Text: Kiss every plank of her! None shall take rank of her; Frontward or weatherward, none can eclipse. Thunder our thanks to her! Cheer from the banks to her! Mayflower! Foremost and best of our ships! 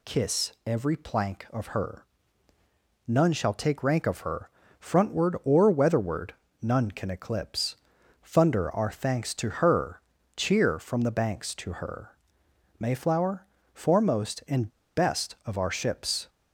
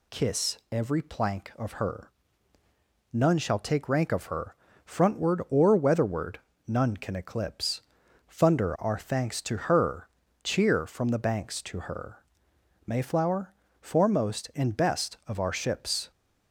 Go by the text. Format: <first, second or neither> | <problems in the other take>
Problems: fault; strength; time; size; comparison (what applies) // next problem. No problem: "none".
second | pauses between "and" and "best"; slight; at 14.6 s; 0.27 s long